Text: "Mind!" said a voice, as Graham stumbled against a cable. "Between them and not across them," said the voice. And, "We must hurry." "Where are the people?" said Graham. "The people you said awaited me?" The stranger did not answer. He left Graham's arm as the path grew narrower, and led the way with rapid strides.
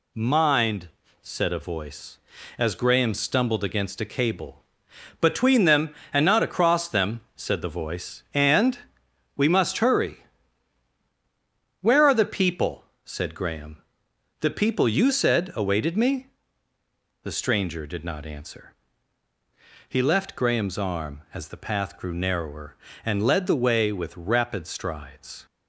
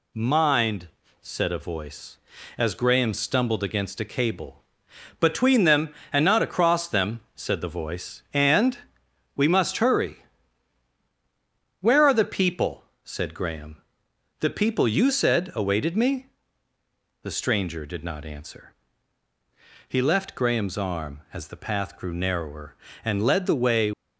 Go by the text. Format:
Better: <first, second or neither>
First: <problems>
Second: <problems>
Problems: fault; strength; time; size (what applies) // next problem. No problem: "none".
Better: first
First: none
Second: stops before "with rapid strides"; at 23.9 s